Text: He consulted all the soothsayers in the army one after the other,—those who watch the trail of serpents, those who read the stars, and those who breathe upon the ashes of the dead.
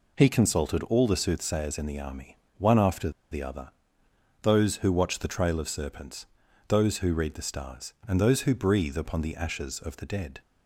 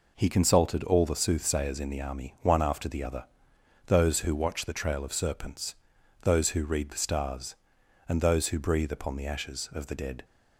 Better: second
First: pauses between "army" and "one"; slight; at 2.3 s; 0.20 s long // pauses between "after" and "the"; slight; at 3.1 s; 0.20 s long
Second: none

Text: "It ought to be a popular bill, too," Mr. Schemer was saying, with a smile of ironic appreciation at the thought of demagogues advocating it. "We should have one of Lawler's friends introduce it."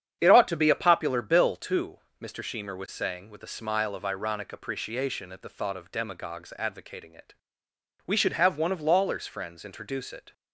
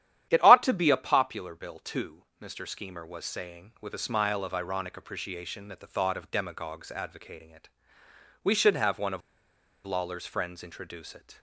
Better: first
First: starts louder than the rest; strong; until 1.2 s; 8.5 dB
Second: starts louder than the rest; strong; until 1.3 s; 11.5 dB // pauses between "of" and "Lawler's"; noticeable; at 9.2 s; 0.65 s long

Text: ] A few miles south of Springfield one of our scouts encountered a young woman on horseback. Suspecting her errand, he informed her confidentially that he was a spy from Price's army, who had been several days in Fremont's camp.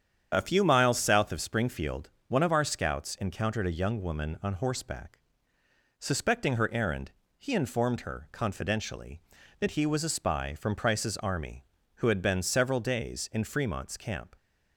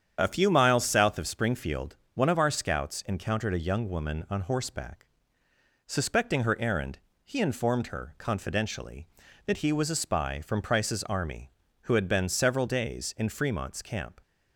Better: neither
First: starts louder than the rest; strong; until 1.3 s; 8.5 dB // pauses between "Springfield" and "one"; slight; at 2.0 s; 0.18 s long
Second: starts louder than the rest; strong; until 1.2 s; 8.5 dB // pauses between "Springfield" and "one"; slight; at 1.9 s; 0.18 s long

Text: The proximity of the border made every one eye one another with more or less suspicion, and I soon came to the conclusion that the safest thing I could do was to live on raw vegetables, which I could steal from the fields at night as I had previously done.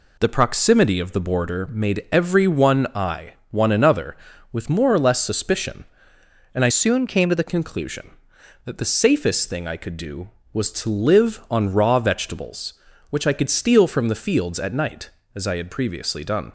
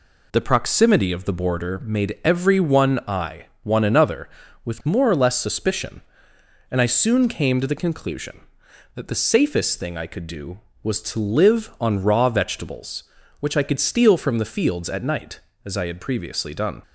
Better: second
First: pauses between "eye" and "one"; slight; at 3.3 s; 0.18 s long // changes voice from "soon" to "the"; from 6.6 to 7.4 s; 0.8 s long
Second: pauses between "eye" and "one"; slight; at 3.4 s; 0.18 s long

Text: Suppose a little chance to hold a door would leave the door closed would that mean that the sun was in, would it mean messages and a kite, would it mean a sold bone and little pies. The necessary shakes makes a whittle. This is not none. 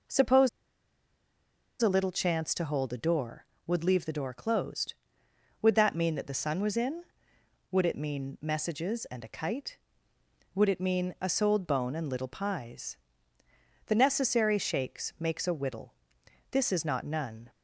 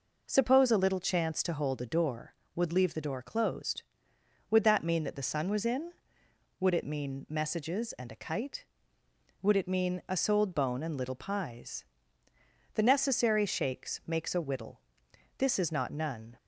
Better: second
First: pauses between "Suppose" and "a"; strong; at 0.4 s; 1.3 s long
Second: none

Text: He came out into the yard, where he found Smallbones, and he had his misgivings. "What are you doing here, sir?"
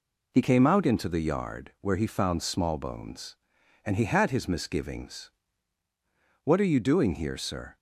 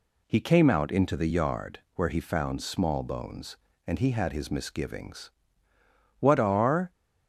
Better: first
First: none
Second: stops before "you doing here sir"; at 6.9 s

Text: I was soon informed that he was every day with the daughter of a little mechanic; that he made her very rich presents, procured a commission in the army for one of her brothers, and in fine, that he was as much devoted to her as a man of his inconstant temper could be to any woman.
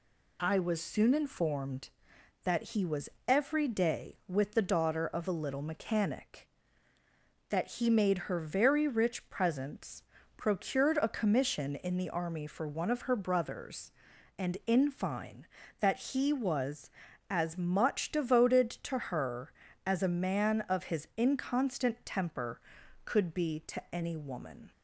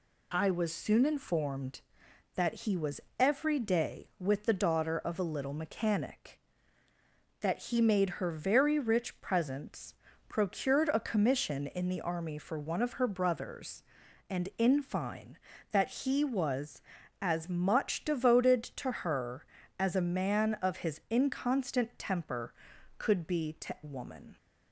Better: first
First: pauses between "was" and "every"; slight; at 3.1 s; 0.18 s long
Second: pauses between "was" and "every"; slight; at 3.0 s; 0.18 s long // skips "any"; at 23.7 s

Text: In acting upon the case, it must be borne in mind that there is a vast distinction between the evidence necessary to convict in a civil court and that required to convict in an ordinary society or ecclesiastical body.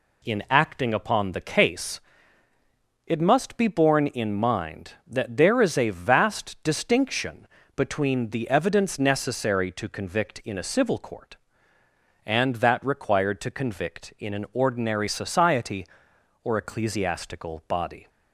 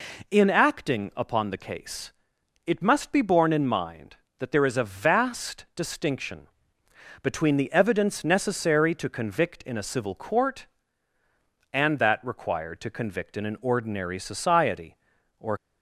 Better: first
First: pauses between "distinction" and "between"; slight; at 7.4 s; 0.28 s long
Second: pauses between "distinction" and "between"; noticeable; at 6.4 s; 0.74 s long // stops before "ecclesiastical body"; at 15.5 s

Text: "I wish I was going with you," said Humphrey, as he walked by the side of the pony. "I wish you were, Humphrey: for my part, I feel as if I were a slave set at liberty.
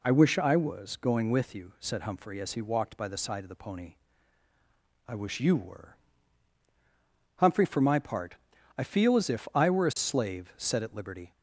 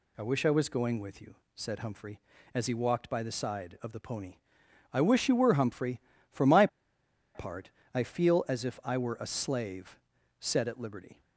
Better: first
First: none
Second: pauses between "my" and "part"; noticeable; at 6.6 s; 0.67 s long // pauses between "slave" and "set"; at 9.9 s; 0.40 s long

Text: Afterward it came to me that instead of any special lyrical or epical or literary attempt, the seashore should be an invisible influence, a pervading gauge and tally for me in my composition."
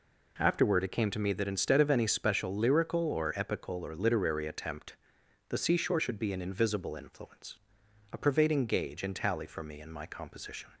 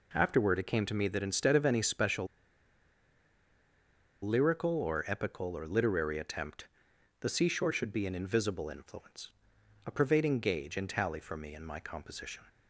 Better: first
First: none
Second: pauses between "special" and "lyrical"; strong; at 2.2 s; 1.9 s long

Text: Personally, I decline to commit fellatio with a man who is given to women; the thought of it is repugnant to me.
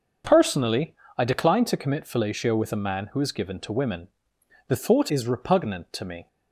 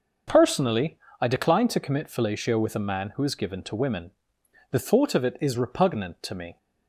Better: second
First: starts louder than the rest; until 1.5 s; 6 dB // skips "of it"; at 5.0 s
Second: starts louder than the rest; noticeable; until 1.5 s; 6 dB

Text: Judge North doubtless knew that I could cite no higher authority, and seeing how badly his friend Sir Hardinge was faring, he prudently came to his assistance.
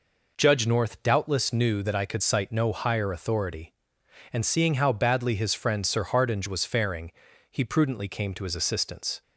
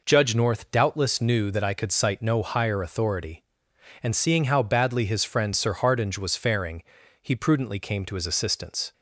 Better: neither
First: none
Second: none

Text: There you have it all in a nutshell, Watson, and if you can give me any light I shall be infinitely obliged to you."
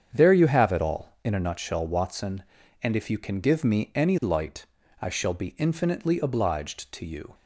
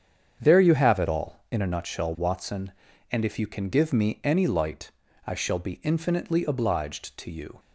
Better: neither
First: starts louder than the rest; strong; until 1.1 s; 8 dB // pauses between "light" and "I"; at 4.6 s; 0.38 s long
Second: starts louder than the rest; strong; until 1.4 s; 8 dB // pauses between "light" and "I"; at 4.8 s; 0.38 s long

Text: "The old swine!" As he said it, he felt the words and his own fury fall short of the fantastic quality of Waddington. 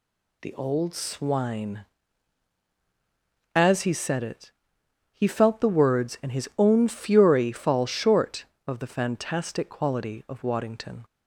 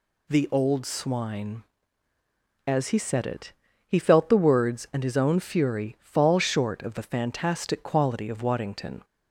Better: neither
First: none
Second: none

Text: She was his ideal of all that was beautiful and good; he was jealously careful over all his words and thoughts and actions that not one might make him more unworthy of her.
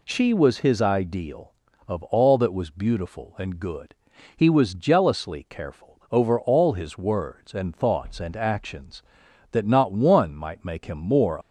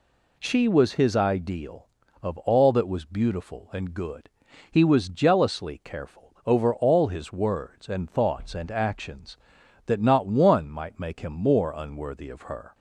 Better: second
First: stops before "unworthy of her"; at 11.4 s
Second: none

